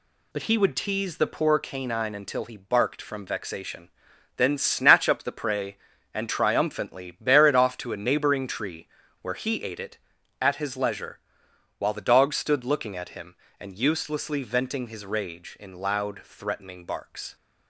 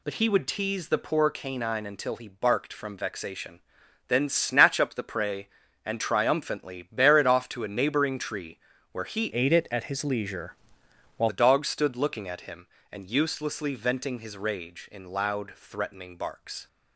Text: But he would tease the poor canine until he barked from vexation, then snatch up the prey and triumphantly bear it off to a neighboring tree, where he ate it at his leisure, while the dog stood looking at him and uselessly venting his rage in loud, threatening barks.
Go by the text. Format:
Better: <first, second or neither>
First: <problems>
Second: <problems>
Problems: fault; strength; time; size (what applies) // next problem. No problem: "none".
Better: first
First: none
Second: changes voice from "ate" to "while"; from 9.3 to 11.2 s; 1.9 s long